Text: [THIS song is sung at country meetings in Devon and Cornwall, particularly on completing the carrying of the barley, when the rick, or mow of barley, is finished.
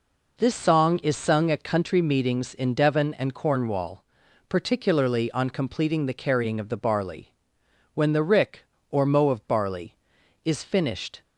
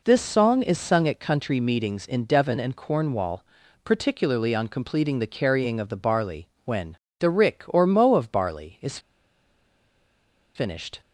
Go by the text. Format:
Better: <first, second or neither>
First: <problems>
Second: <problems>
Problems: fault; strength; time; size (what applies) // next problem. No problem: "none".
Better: first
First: none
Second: pauses between "when" and "the"; slight; at 6.9 s; 0.24 s long // pauses between "is" and "finished"; strong; at 8.9 s; 1.5 s long